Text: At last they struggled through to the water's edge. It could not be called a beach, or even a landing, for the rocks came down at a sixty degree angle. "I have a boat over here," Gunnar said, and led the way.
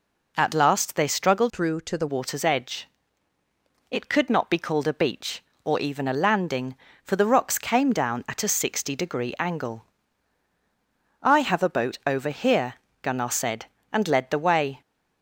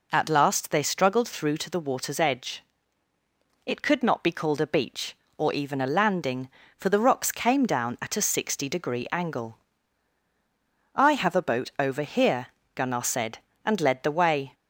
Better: second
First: changes voice from "through" to "the"; from 1.5 to 2.0 s; 0.5 s long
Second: none

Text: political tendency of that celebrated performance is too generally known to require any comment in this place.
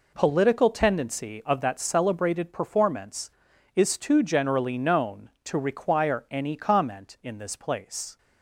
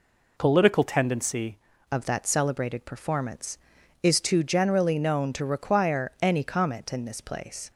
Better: first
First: none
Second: changes voice at "of"; from 1.9 s on; 5.8 s long

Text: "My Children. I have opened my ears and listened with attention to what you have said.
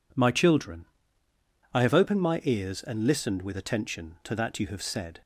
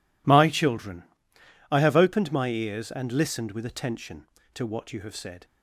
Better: second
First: says "that" for "what"; at 4.3 s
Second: none

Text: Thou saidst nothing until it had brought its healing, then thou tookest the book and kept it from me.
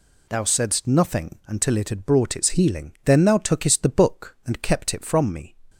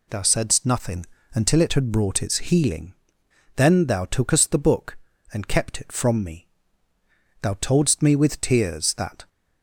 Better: first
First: none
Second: pauses between "nothing" and "until"; slight; at 1.0 s; 0.28 s long // goes on to say "Thou toldst me with tears that"; strong; from 7.4 s on; 1.8 s long

